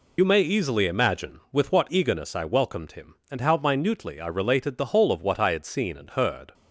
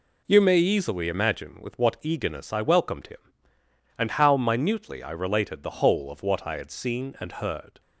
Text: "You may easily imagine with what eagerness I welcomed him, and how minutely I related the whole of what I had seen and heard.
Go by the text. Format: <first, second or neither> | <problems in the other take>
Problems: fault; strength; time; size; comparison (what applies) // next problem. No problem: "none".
second | loses the start of "You"; at 0.1 s; 55 ms